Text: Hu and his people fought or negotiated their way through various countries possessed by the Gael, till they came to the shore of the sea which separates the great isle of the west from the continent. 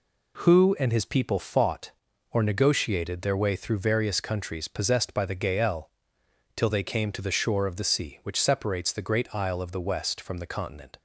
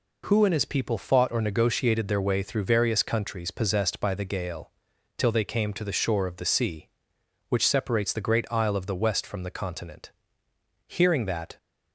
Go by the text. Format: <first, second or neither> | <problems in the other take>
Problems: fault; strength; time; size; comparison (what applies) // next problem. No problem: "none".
first | goes on to say "Hearing that"; noticeable; from 10.8 s on; 0.70 s long